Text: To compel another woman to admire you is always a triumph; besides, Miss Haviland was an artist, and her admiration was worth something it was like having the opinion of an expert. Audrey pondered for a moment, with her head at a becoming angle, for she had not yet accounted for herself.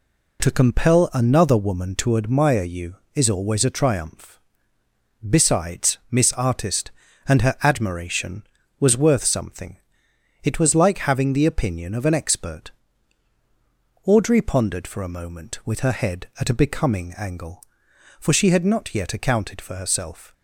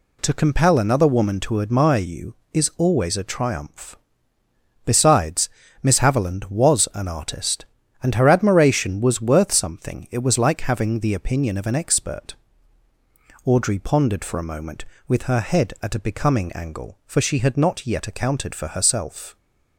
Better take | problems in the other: second | skips "Haviland was an"; at 6.3 s // pauses between "something" and "it"; noticeable; at 9.7 s; 0.66 s long

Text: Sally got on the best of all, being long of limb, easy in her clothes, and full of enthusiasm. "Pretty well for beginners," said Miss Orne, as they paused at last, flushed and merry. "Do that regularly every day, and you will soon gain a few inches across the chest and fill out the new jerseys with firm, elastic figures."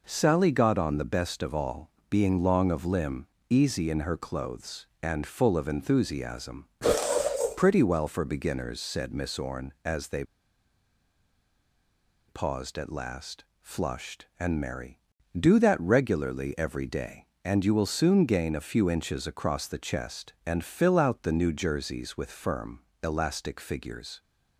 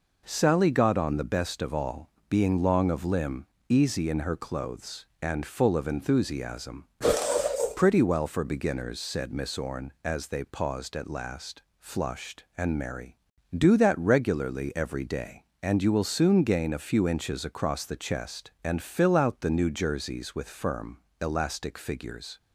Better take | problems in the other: second | pauses between "they" and "paused"; strong; at 10.2 s; 2.0 s long

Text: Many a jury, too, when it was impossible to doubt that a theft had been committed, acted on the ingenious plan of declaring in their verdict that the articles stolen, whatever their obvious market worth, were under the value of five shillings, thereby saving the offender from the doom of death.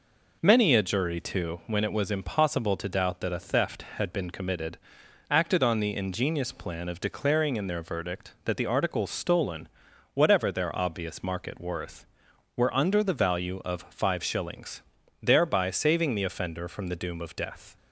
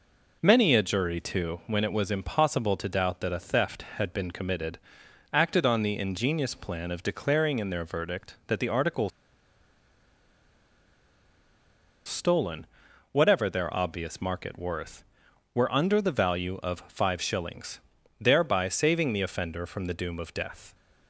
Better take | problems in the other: first | pauses between "articles" and "stolen"; strong; at 9.1 s; 2.9 s long

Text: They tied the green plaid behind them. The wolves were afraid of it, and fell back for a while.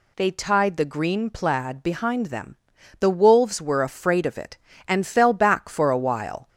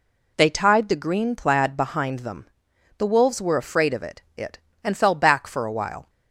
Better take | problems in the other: first | says "it" twice; at 4.3 s

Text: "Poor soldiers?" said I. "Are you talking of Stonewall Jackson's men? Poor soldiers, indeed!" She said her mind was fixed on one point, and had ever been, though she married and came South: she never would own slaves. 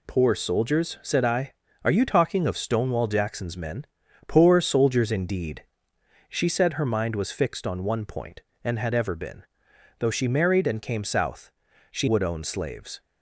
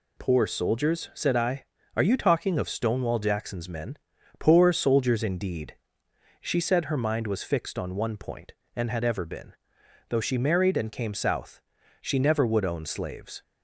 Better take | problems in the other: second | skips "never"; at 12.0 s

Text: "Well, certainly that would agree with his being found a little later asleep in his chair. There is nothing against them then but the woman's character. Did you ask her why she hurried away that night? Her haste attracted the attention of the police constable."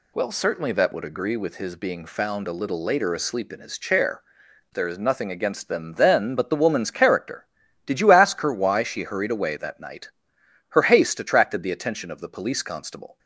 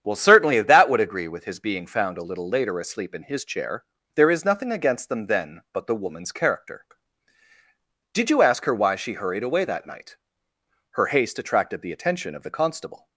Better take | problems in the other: first | starts louder than the rest; strong; until 1.0 s; 8.5 dB // skips "police"; at 12.5 s

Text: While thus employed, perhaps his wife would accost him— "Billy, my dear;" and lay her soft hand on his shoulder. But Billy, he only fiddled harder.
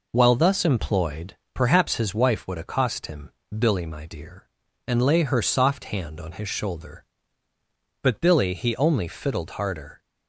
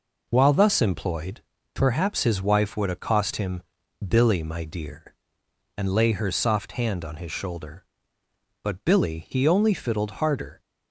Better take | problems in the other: neither | none

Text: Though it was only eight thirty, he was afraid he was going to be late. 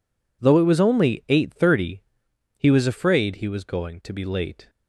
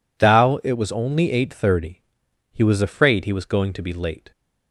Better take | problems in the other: first | says "Thou" for "Though"; at 0.1 s

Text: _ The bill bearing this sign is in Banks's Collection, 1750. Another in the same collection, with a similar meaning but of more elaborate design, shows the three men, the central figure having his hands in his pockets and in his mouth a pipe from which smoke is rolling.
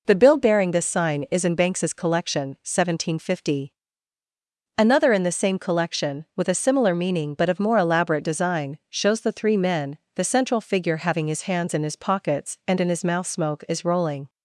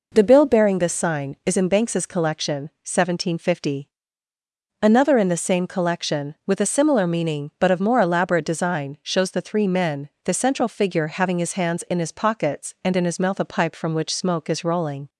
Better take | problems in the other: second | skips "a pipe from which"; at 13.2 s

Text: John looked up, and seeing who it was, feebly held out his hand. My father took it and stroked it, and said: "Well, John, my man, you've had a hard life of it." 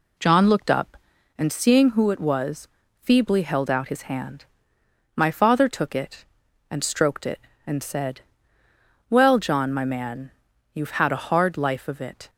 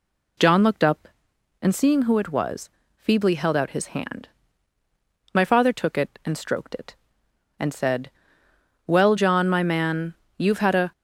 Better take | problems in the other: first | stops before "hard life of it"; at 10.9 s

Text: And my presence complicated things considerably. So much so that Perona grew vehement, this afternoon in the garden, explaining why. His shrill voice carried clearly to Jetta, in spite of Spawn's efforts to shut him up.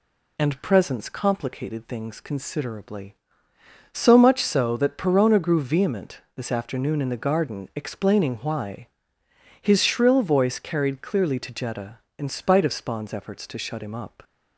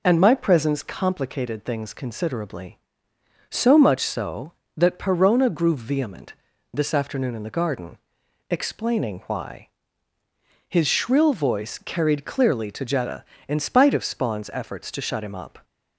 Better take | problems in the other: second | skips "my"; at 0.6 s

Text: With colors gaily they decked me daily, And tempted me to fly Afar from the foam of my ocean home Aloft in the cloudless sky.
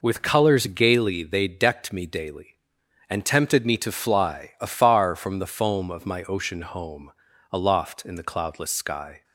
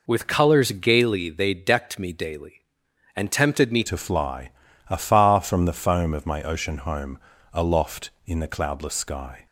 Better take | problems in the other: first | changes voice at "to"; from 3.8 s on; 5.6 s long // pauses between "fly" and "Afar"; at 4.4 s; 0.40 s long // pauses between "home" and "Aloft"; slight; at 7.1 s; 0.36 s long; also in the first

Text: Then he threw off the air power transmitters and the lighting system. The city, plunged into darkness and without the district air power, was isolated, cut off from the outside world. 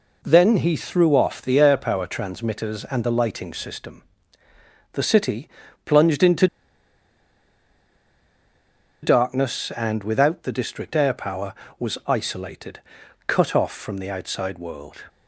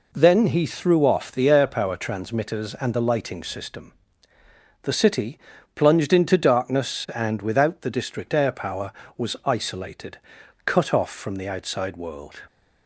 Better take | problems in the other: second | pauses between "into" and "darkness"; strong; at 6.4 s; 2.5 s long

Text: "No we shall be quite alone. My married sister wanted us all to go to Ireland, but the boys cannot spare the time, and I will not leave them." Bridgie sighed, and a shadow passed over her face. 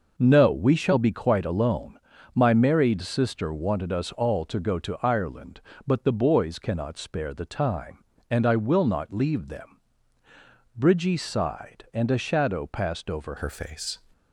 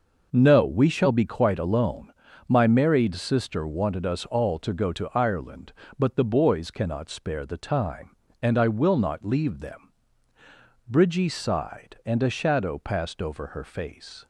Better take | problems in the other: second | changes voice at "her"; from 13.3 s on; 0.6 s long

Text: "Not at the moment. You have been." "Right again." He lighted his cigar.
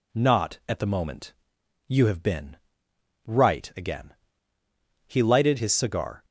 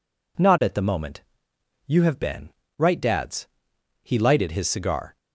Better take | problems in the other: first | says "dads" for "again"; at 3.0 s

